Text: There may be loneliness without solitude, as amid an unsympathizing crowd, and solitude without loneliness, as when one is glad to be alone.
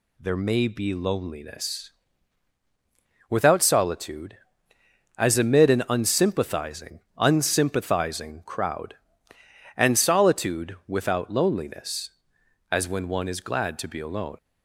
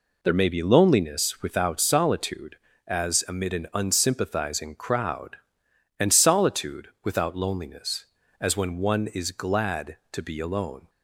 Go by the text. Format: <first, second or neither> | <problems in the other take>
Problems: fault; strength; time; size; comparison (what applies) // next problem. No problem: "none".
second | pauses between "loneliness" and "without"; strong; at 1.9 s; 1.3 s long // says "unsympathizing" twice; at 7.1 s